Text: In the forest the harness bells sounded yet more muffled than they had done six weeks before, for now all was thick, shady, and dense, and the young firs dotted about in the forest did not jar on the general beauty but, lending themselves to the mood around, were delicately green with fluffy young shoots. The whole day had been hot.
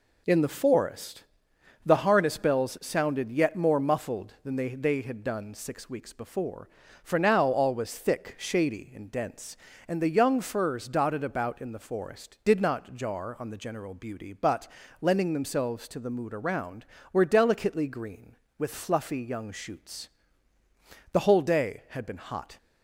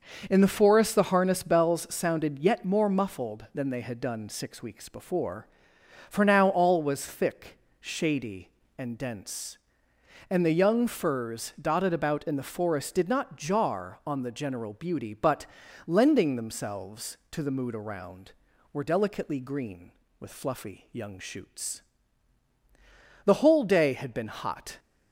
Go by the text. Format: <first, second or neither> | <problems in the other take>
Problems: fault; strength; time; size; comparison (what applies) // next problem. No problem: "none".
second | pauses between "forest" and "the"; noticeable; at 1.2 s; 0.60 s long // says "they" twice; at 4.6 s